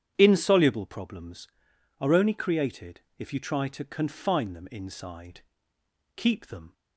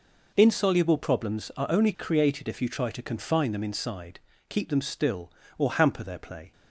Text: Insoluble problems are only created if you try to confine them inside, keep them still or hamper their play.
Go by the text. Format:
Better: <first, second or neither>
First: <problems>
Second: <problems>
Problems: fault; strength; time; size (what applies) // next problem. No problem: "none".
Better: second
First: starts louder than the rest; strong; until 1.1 s; 9 dB // pauses between "created" and "if"; slight; at 3.0 s; 0.18 s long // stops before "still or hamper their play"; at 6.7 s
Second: none